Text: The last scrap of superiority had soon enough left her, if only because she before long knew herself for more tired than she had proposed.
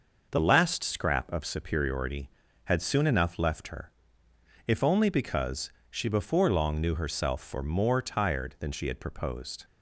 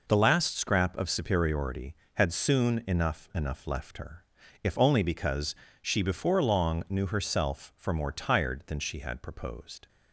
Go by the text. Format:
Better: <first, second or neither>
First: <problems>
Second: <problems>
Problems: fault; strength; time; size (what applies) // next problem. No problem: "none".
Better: first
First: pauses between "because" and "she"; slight; at 5.7 s; 0.18 s long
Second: says "enough" twice; at 3.3 s // pauses between "because" and "she"; slight; at 5.5 s; 0.26 s long